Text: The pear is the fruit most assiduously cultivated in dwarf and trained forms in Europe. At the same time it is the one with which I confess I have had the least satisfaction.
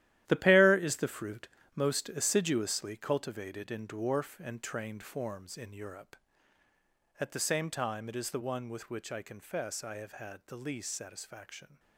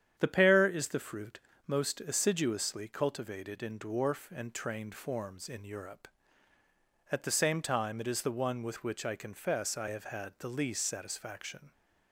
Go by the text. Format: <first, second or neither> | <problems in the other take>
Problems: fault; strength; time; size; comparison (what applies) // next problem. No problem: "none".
second | gets quieter; strong; throughout; 10.5 dB // starts louder than the rest; strong; until 1.2 s; 13 dB; strong in the second // pauses between "fruit" and "most"; slight; at 1.4 s; 0.28 s long; slight in the second